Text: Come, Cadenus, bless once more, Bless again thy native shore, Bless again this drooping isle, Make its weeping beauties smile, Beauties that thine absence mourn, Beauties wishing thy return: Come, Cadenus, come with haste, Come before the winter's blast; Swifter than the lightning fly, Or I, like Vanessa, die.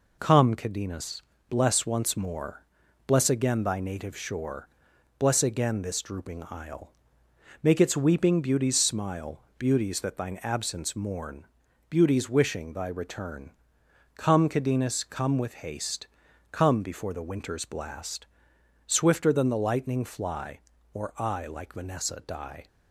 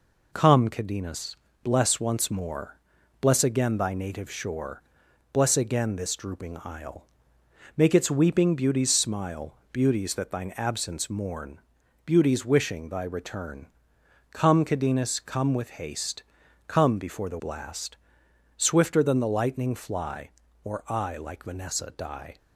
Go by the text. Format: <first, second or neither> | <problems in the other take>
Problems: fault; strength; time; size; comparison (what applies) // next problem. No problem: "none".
first | skips "winter's"; at 17.3 s